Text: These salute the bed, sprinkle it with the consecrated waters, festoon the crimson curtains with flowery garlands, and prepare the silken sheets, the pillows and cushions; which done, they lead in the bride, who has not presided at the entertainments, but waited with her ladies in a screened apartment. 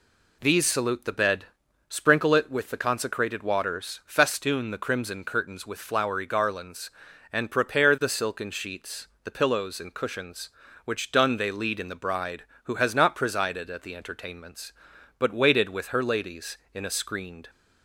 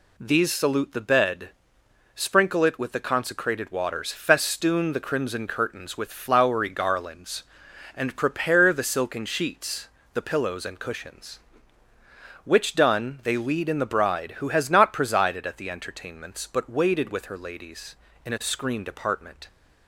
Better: second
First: stops before "apartment"; at 17.4 s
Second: none

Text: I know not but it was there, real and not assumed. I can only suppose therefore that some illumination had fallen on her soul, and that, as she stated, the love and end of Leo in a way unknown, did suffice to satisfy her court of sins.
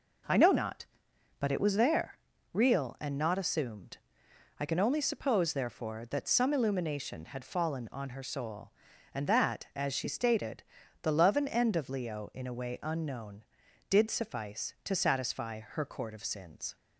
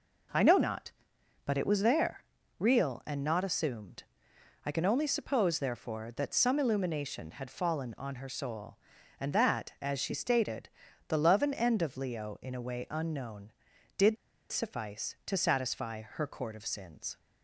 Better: first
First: none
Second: pauses between "did" and "suffice"; slight; at 14.1 s; 0.34 s long

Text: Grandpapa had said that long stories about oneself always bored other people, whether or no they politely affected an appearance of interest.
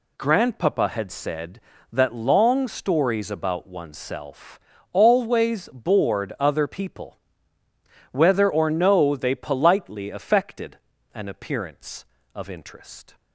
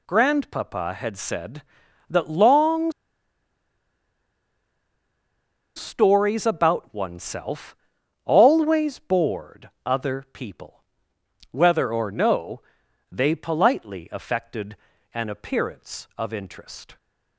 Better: first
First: pauses between "oneself" and "always"; slight; at 4.5 s; 0.36 s long // pauses between "affected" and "an"; at 10.7 s; 0.38 s long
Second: pauses between "long" and "stories"; strong; at 2.9 s; 2.8 s long // pauses between "oneself" and "always"; noticeable; at 7.7 s; 0.48 s long // pauses between "bored" and "other"; slight; at 9.6 s; 0.16 s long // pauses between "no" and "they"; noticeable; at 12.6 s; 0.50 s long // pauses between "affected" and "an"; at 14.7 s; 0.38 s long

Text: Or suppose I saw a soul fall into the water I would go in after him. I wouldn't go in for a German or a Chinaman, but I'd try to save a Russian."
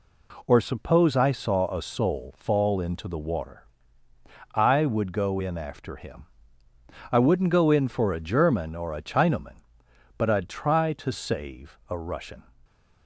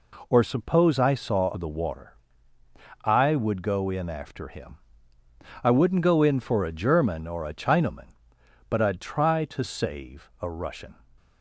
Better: first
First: pauses between "water" and "I"; noticeable; at 3.6 s; 0.88 s long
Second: skips "a soul fall into"; at 1.5 s // pauses between "water" and "I"; noticeable; at 2.1 s; 0.88 s long

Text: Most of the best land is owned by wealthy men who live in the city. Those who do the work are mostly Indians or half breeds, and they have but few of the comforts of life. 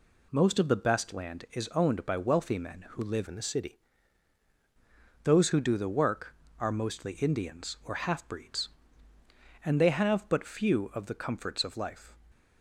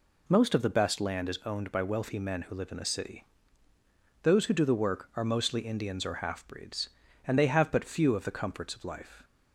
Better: second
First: changes voice from "in" to "city"; from 3.2 to 3.7 s; 0.5 s long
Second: none

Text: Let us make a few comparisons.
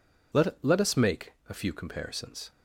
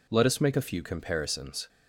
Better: second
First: says "Let" twice; at 0.6 s // pauses between "make" and "a"; slight; at 1.3 s; 0.17 s long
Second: none

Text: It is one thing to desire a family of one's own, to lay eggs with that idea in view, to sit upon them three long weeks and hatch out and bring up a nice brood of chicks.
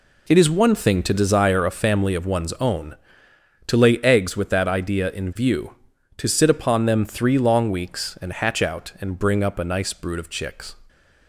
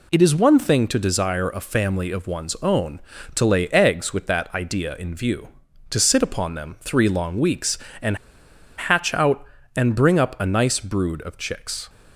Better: first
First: none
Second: pauses between "and" and "hatch"; noticeable; at 8.1 s; 0.60 s long

